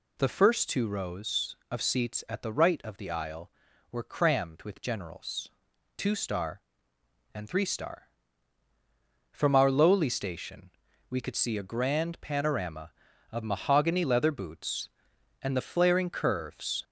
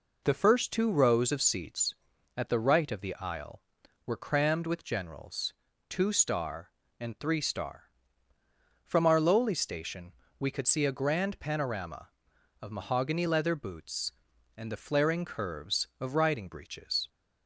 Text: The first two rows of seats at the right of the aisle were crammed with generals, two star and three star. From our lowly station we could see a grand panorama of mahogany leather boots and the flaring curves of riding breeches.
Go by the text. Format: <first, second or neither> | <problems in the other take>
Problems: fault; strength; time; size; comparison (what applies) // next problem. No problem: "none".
second | pauses between "station" and "we"; at 10.6 s; 0.40 s long; slight in the second // stops before "of riding breeches"; at 16.8 s